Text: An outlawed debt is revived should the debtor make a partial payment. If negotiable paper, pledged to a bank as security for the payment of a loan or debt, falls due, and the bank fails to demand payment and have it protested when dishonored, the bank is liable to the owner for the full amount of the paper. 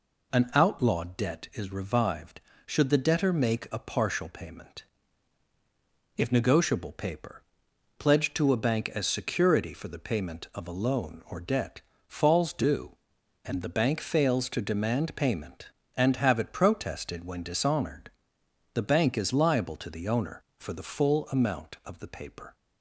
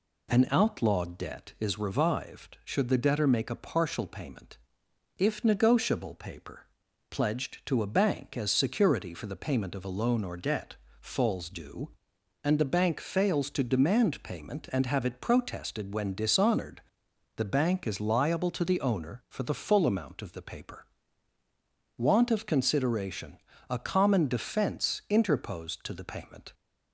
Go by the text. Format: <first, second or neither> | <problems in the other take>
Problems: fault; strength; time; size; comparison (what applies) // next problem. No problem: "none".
first | goes on to say "Want of consideration a common defense interposed to the payment"; strong; from 21.9 s on; 4.5 s long